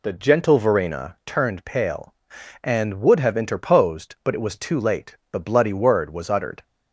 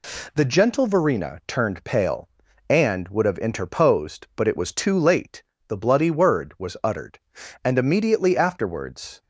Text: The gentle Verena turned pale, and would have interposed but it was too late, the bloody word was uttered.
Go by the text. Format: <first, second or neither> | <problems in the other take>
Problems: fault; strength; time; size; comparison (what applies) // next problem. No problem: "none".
first | goes on to say "And immediately afterwards"; from 7.6 s on; 1.5 s long